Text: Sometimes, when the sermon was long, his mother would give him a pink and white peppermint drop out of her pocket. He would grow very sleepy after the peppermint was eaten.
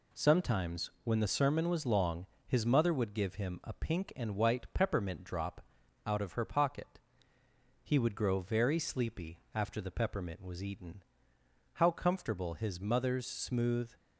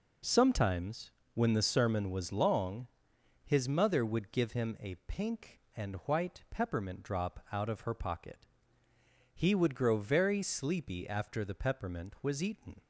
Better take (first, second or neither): second